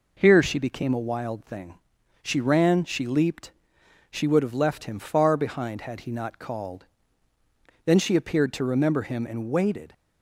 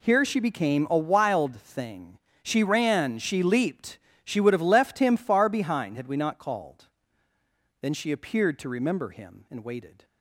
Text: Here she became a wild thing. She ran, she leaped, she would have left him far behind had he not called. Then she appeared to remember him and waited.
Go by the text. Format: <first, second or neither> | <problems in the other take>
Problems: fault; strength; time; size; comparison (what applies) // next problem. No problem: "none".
first | says "we" for "he"; at 6.0 s